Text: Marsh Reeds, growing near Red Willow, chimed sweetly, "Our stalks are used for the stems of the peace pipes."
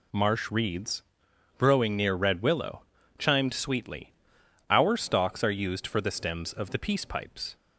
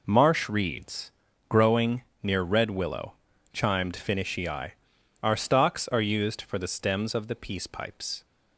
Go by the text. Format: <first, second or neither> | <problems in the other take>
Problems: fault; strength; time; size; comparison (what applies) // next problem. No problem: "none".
first | pauses between "growing" and "near"; slight; at 2.0 s; 0.18 s long // says "finishii" for "sweetly"; at 3.9 s